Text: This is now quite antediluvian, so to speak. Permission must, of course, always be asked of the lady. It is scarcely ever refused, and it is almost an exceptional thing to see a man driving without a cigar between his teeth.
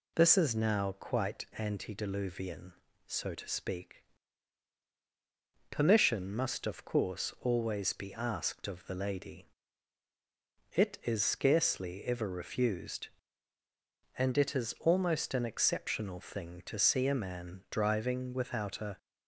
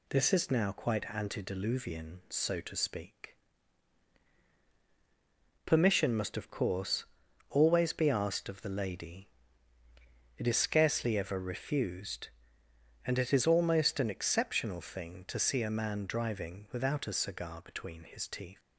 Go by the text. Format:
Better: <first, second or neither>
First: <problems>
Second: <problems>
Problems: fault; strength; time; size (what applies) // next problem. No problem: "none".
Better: second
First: stops before "cigar between his teeth"; at 18.9 s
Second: none